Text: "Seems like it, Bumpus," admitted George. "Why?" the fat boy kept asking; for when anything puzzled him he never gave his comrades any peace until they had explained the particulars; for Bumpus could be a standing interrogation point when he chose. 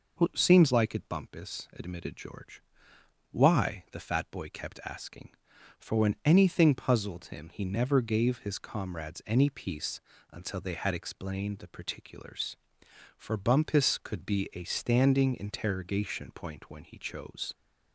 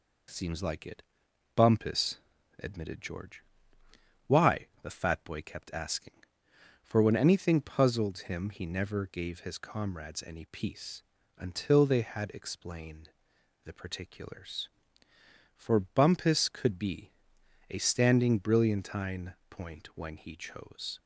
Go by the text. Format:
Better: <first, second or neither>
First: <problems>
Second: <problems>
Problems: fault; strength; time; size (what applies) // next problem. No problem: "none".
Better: first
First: pauses between "peace" and "until"; slight; at 9.9 s; 0.32 s long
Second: pauses between "peace" and "until"; at 11.0 s; 0.38 s long // pauses between "explained" and "the"; noticeable; at 13.0 s; 0.54 s long // pauses between "be" and "a"; noticeable; at 17.1 s; 0.60 s long // says "brilliantine" for "interrogation"; at 18.3 s